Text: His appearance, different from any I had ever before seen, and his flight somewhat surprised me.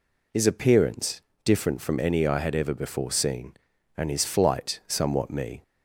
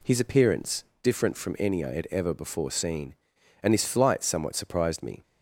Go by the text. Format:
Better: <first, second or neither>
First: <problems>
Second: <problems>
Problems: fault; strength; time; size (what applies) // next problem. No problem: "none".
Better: second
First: skips "surprised"; at 5.3 s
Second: none